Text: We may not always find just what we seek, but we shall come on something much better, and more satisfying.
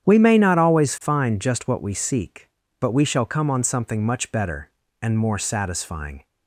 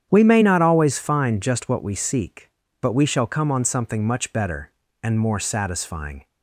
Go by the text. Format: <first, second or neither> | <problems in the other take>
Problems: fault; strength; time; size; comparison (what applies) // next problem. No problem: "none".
neither | starts louder than the rest; strong; the same in both